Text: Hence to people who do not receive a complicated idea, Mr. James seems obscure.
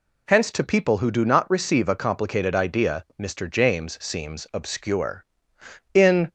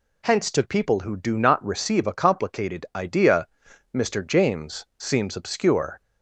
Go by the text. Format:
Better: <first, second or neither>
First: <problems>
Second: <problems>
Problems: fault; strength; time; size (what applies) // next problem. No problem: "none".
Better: second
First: goes on to say "In"; slight; from 5.9 s on; 0.40 s long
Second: none